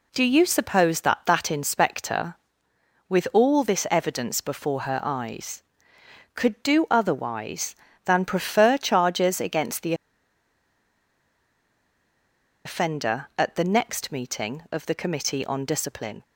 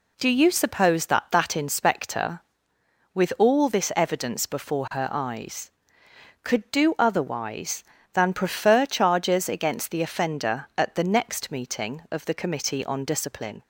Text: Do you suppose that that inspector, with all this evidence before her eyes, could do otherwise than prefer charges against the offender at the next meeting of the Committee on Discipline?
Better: second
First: pauses between "the" and "offender"; strong; at 9.9 s; 2.7 s long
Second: none

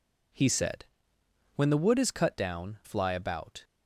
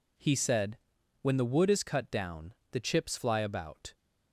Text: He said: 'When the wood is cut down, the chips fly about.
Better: second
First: skips "the chips"; at 2.8 s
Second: none

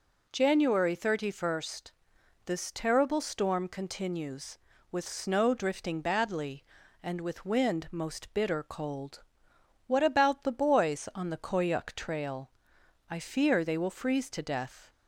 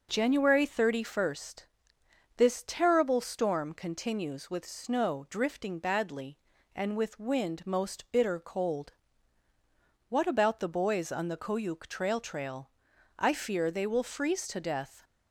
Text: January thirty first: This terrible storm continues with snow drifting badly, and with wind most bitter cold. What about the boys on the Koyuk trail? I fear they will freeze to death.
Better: first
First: none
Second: starts louder than the rest; noticeable; until 1.1 s; 6 dB // says "trail" twice; at 12.1 s

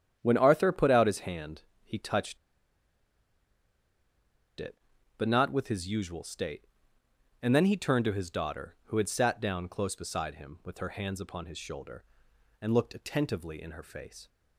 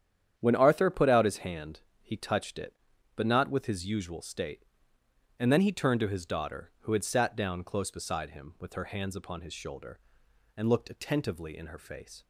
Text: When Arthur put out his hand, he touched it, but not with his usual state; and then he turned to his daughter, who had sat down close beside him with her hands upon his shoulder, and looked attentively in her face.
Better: second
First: starts louder than the rest; strong; until 1.2 s; 9.5 dB // pauses between "touched" and "it"; strong; at 2.3 s; 2.2 s long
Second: starts louder than the rest; strong; until 1.3 s; 9.5 dB

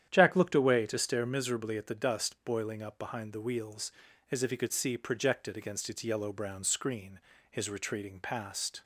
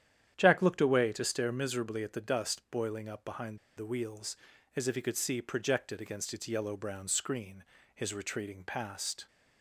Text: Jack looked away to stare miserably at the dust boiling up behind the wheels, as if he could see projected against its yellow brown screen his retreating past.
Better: first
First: starts louder than the rest; strong; until 1.1 s; 10 dB // pauses between "screen" and "his"; slight; at 7.1 s; 0.32 s long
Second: starts louder than the rest; strong; until 1.3 s; 10 dB // pauses between "behind" and "the"; slight; at 3.5 s; 0.18 s long // pauses between "screen" and "his"; slight; at 7.6 s; 0.32 s long

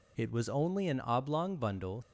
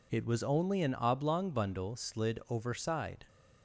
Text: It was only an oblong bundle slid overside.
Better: second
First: stops before "slid overside"; at 2.0 s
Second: none

